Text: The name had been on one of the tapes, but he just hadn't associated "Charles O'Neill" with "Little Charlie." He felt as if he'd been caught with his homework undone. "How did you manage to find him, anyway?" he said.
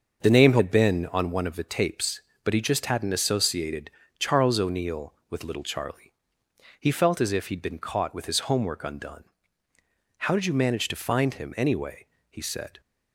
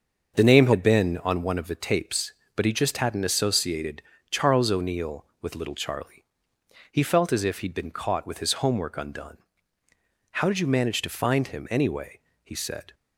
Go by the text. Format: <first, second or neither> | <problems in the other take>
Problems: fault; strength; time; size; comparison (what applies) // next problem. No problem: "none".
neither | starts louder than the rest; the same in both // pauses between "associated" and "Charles"; slight; the same in both